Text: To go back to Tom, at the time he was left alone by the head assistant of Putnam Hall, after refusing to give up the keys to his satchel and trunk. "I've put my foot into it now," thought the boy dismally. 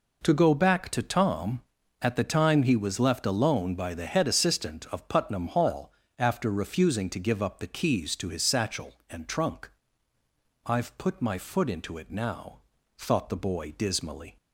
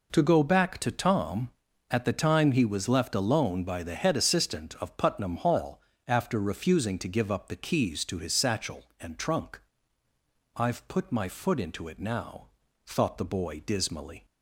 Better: neither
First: none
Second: none

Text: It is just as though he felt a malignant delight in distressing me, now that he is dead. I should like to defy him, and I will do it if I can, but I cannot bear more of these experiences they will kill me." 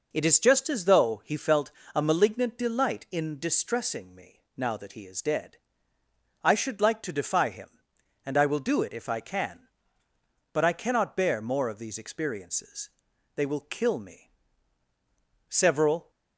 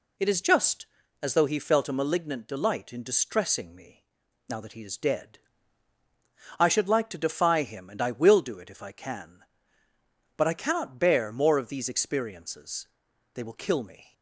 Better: second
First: pauses between "felt" and "a"; slight; at 1.7 s; 0.22 s long // pauses between "experiences" and "they"; noticeable; at 12.8 s; 0.46 s long // goes on to say "Several"; noticeable; from 15.4 s on; 0.62 s long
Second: pauses between "experiences" and "they"; noticeable; at 12.8 s; 0.48 s long

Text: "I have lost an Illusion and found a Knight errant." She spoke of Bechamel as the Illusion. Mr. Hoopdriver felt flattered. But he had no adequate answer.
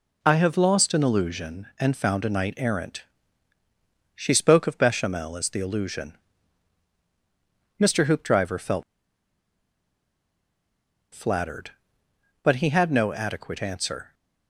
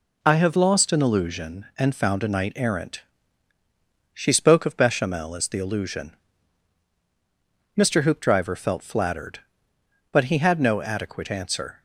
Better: second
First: pauses between "felt" and "flattered"; strong; at 8.8 s; 2.3 s long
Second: none

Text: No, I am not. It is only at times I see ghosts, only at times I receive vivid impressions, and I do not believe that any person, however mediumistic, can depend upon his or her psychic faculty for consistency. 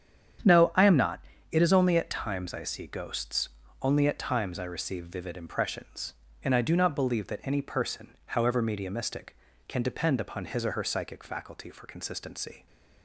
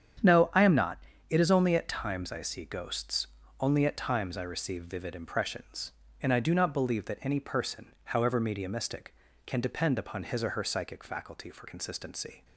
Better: neither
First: starts louder than the rest; strong; until 1.7 s; 8.5 dB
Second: starts louder than the rest; strong; until 1.5 s; 8.5 dB

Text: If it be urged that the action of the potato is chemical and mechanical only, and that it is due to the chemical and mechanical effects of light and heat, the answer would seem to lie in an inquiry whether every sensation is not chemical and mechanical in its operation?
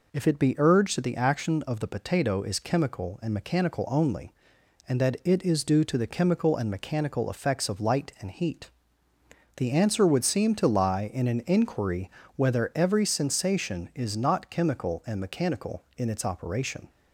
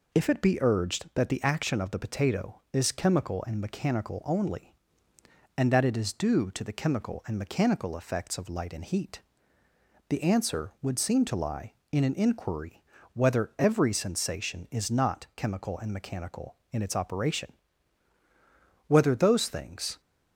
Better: first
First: pauses between "inquiry" and "whether"; slight; at 12.0 s; 0.26 s long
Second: pauses between "inquiry" and "whether"; slight; at 12.8 s; 0.32 s long // goes on to say "whether those things"; noticeable; from 18.9 s on; 1.0 s long

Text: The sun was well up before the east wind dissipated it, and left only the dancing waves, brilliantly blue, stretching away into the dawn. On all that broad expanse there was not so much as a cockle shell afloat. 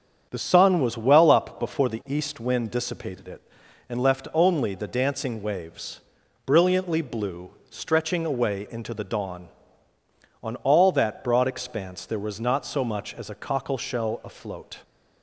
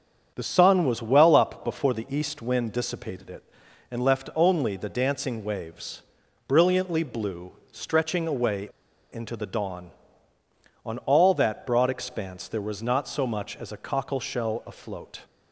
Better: first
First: starts louder than the rest; strong; until 1.3 s; 7.5 dB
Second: starts louder than the rest; strong; until 1.3 s; 7.5 dB // pauses between "away" and "into"; at 8.6 s; 0.42 s long

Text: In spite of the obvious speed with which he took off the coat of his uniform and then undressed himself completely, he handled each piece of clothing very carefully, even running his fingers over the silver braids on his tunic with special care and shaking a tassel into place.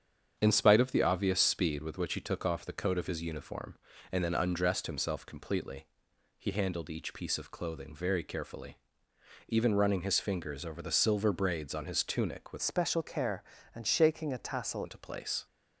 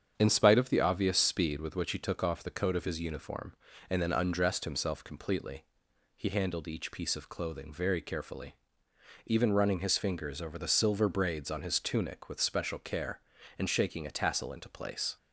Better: second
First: starts louder than the rest; strong; until 1.4 s; 8 dB // changes voice from "special" to "tassel"; from 12.6 to 14.8 s; 2.2 s long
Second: starts louder than the rest; strong; until 1.1 s; 8 dB

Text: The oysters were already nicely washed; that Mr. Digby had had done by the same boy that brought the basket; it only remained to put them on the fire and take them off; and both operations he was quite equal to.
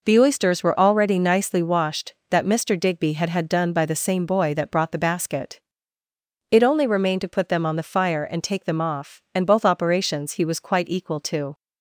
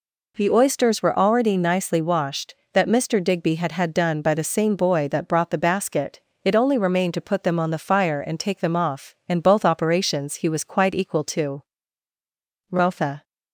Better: first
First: none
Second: goes on to say "Rotha"; from 12.6 s on; 0.54 s long

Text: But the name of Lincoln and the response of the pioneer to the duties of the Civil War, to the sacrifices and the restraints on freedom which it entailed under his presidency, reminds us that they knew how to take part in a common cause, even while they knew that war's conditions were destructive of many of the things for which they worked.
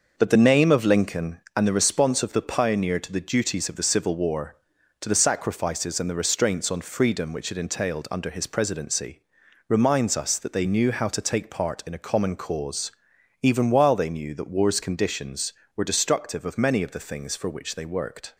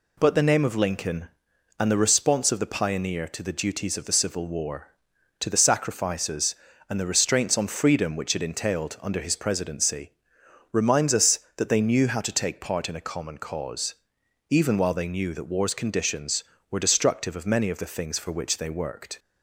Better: second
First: starts louder than the rest; noticeable; until 1.5 s; 6 dB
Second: none

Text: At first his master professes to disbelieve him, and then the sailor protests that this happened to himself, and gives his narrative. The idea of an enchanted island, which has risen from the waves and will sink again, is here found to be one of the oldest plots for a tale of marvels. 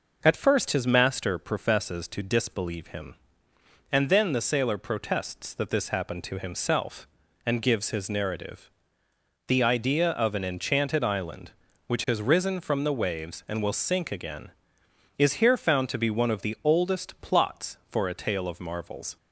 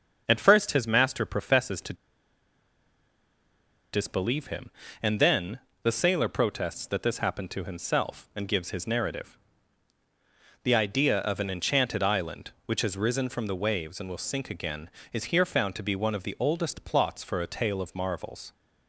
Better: first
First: none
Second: starts louder than the rest; until 1.2 s; 6.5 dB // pauses between "to" and "disbelieve"; strong; at 1.9 s; 1.9 s long // pauses between "then" and "the"; slight; at 5.6 s; 0.22 s long

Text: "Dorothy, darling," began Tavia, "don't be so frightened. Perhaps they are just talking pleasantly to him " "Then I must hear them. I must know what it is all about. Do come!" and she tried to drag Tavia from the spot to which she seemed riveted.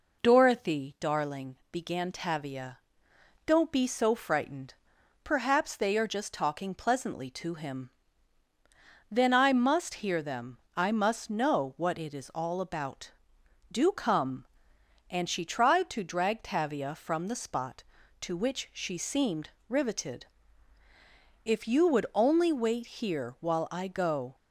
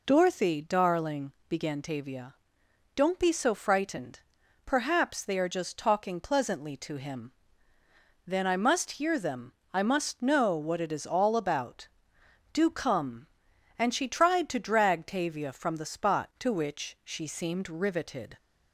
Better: second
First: pauses between "seemed" and "riveted"; slight; at 19.5 s; 0.18 s long // goes on to say "If you would only wait here while I go"; strong; from 21.4 s on; 2.9 s long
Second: none

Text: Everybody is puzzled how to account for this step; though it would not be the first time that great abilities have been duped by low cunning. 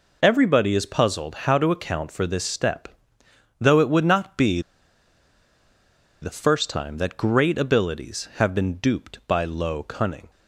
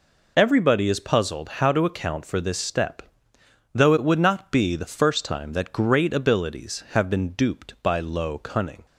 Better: second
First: pauses between "be" and "the"; strong; at 4.6 s; 1.5 s long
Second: none

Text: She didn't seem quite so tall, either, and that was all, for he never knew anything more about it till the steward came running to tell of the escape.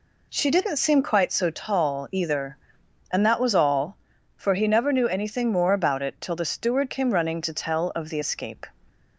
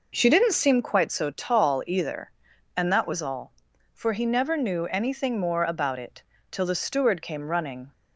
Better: first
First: none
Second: pauses between "it" and "till"; slight; at 6.2 s; 0.28 s long // stops before "to tell of the escape"; at 7.9 s

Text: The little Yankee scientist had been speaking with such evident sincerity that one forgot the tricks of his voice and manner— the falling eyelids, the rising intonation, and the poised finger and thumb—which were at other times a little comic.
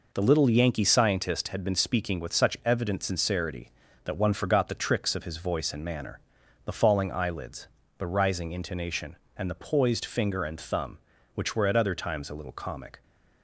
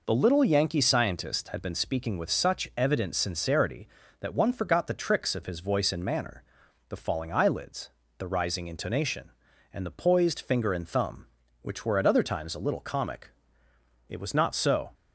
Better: first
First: none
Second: goes on to say "It was not so"; noticeable; from 14.0 s on; 0.86 s long

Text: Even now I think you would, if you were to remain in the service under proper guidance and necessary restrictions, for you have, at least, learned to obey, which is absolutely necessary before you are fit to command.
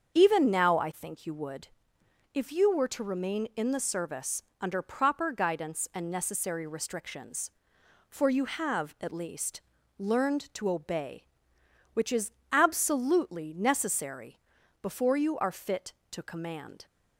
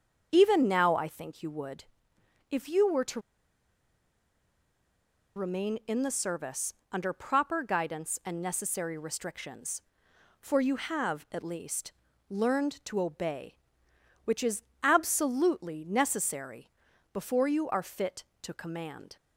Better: first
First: starts louder than the rest; until 1.1 s; 7 dB // pauses between "service" and "under"; slight; at 4.4 s; 0.18 s long // pauses between "is" and "absolutely"; slight; at 12.3 s; 0.20 s long // pauses between "necessary" and "before"; at 14.3 s; 0.42 s long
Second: starts louder than the rest; until 1.3 s; 7 dB // pauses between "to" and "remain"; strong; at 3.1 s; 2.1 s long // pauses between "service" and "under"; slight; at 6.7 s; 0.18 s long // pauses between "is" and "absolutely"; slight; at 14.6 s; 0.20 s long // pauses between "necessary" and "before"; at 16.7 s; 0.42 s long

